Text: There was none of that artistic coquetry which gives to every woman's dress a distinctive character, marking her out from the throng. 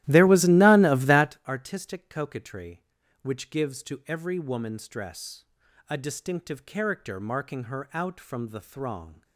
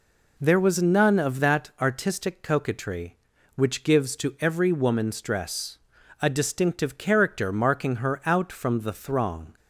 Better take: second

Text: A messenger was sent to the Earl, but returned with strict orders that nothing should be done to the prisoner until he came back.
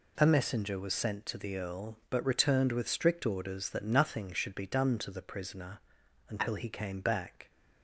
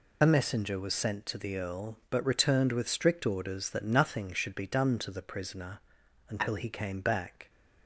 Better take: first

